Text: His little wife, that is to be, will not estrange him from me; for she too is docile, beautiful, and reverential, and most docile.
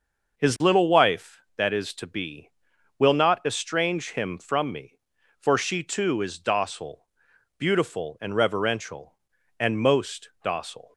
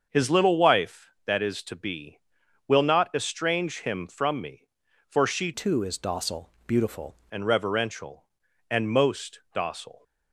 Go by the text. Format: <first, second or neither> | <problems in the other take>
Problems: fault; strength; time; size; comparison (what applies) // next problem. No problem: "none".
first | starts louder than the rest; until 1.1 s; 6.5 dB // changes voice from "too" to "beautiful"; from 5.5 to 7.1 s; 1.6 s long